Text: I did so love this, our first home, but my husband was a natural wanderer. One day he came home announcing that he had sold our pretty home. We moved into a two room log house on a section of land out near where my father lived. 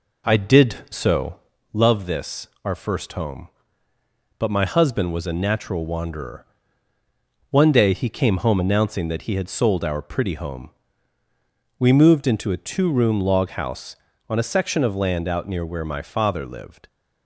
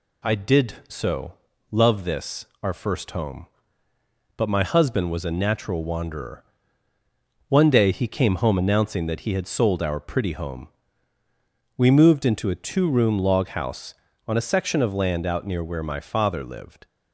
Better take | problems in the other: second | starts louder than the rest; noticeable; until 1.6 s; 4 dB // pauses between "so" and "love"; slight; at 1.3 s; 0.36 s long; slight in the second

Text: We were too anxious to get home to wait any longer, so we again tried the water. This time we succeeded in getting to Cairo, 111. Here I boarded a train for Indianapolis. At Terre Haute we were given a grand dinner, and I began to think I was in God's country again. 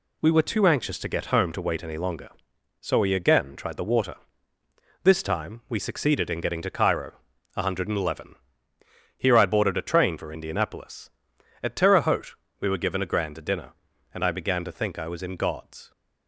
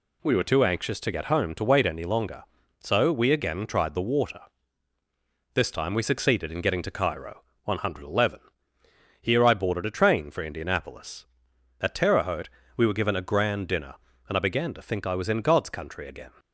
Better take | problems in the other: second | pauses between "Haute" and "we"; slight; at 12.3 s; 0.26 s long; slight in the second // stops before "country again"; at 15.9 s

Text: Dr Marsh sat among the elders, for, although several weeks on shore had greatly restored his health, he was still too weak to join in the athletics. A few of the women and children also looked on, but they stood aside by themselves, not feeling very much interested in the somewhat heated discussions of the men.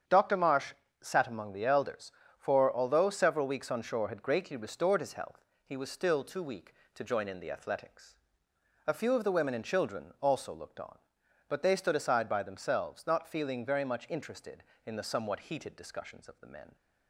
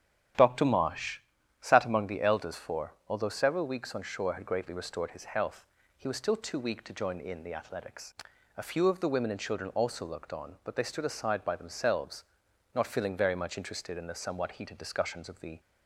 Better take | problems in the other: first | starts louder than the rest; strong; until 1.7 s; 11 dB; strong in the first // pauses between "Marsh" and "sat"; at 1.1 s; 0.42 s long; slight in the first // stops before "men"; at 15.5 s

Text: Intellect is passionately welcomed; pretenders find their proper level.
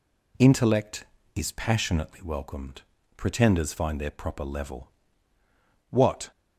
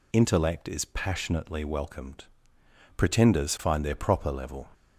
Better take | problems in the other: second | goes on to say "What"; slight; from 5.9 s on; 0.40 s long

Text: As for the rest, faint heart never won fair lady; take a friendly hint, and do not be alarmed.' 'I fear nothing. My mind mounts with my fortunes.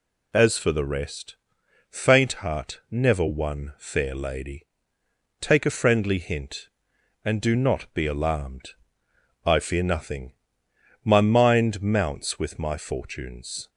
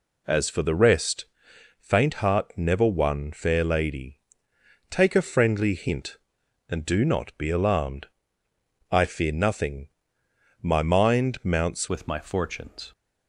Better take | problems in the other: first | changes voice at "with"; from 11.8 s on; 1.1 s long

